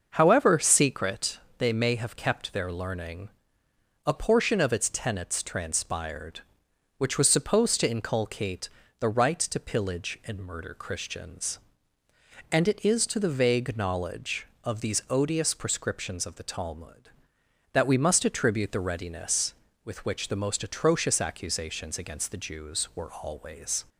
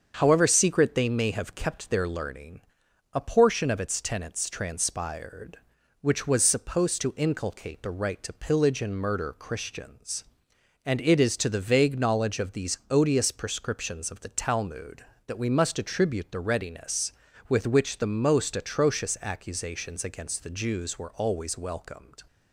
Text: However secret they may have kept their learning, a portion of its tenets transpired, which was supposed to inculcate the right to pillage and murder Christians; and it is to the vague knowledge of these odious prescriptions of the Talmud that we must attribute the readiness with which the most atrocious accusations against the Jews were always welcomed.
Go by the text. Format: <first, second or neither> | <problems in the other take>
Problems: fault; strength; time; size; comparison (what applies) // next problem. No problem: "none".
second | starts louder than the rest; until 1.1 s; 6.5 dB; also in the second // pauses between "secret" and "they"; slight; at 1.3 s; 0.22 s long // pauses between "inculcate" and "the"; slight; at 8.6 s; 0.28 s long // stops before "welcomed"; at 23.8 s